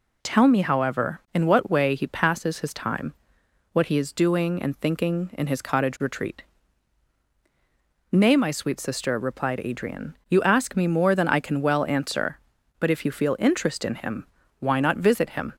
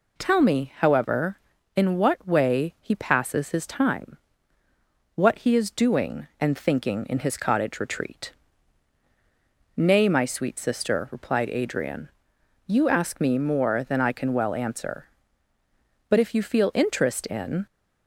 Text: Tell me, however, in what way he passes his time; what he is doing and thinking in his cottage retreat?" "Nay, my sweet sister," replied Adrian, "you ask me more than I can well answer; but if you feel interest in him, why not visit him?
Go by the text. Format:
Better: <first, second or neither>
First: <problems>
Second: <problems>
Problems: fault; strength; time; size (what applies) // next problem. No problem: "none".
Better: first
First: none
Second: stops before "him why not visit him"; at 17.6 s